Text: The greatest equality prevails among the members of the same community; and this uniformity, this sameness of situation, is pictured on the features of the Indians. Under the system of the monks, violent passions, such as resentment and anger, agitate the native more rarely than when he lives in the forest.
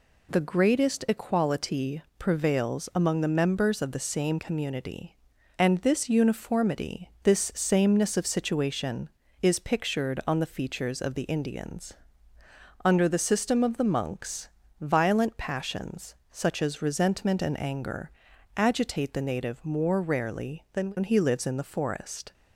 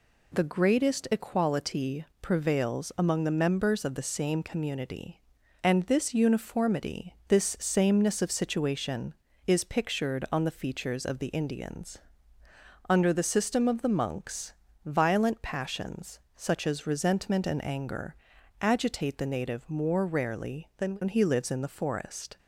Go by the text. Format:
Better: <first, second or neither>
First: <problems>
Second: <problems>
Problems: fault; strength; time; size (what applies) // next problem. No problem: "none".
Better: neither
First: pauses between "equality" and "prevails"; slight; at 2.0 s; 0.18 s long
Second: pauses between "equality" and "prevails"; slight; at 2.0 s; 0.18 s long